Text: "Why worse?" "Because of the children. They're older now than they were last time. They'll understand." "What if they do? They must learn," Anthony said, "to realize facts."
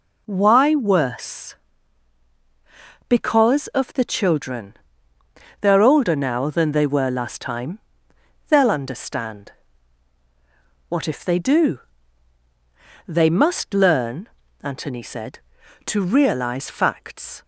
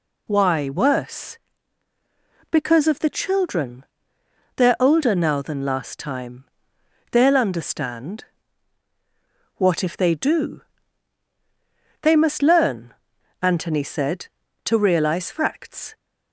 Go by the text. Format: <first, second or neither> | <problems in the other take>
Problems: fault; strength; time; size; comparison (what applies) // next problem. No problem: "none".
first | skips "they were"; at 5.6 s